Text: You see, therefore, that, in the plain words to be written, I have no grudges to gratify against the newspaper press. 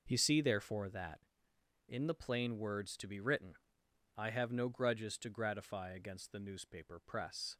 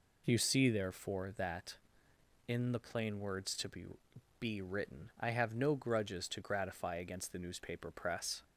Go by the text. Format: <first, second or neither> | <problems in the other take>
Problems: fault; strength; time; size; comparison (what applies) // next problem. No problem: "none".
first | says "be" twice; at 4.3 s